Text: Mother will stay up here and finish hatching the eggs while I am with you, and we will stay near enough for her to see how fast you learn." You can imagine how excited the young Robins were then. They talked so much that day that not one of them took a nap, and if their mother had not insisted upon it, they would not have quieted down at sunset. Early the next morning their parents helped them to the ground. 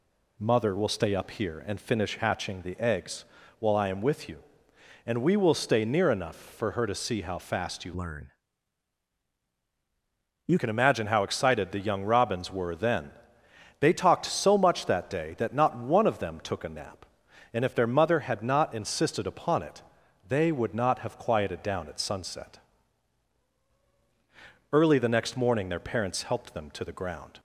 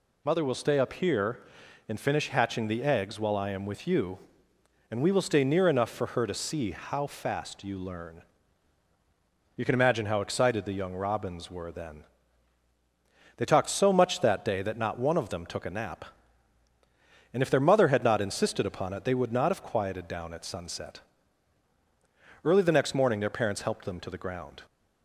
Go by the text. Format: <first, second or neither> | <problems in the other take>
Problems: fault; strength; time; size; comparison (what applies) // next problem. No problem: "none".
second | pauses between "eggs" and "while"; slight; at 3.2 s; 0.34 s long // changes voice from "learn" to "You"; from 7.9 to 10.5 s; 2.6 s long